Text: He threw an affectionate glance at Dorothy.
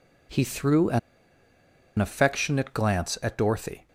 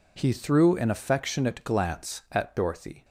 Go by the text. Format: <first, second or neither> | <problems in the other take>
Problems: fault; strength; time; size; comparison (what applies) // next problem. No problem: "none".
second | pauses between "an" and "affectionate"; at 0.9 s; 0.99 s long